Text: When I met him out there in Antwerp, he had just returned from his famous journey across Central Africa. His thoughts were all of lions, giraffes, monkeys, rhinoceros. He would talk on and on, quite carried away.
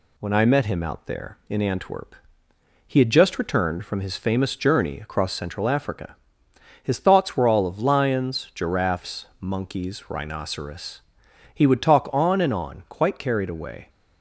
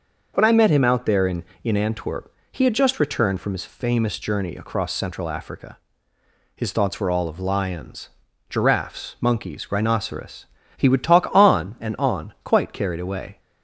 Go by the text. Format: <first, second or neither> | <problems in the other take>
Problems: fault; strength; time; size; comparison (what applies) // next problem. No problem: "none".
first | says "in" twice; at 1.6 s